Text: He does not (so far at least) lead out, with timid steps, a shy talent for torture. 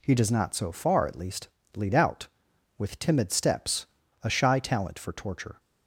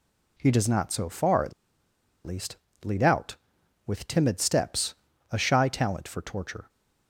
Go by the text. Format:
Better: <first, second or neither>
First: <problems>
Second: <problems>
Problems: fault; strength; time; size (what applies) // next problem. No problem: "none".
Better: first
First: none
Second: pauses between "at" and "least"; noticeable; at 1.5 s; 0.73 s long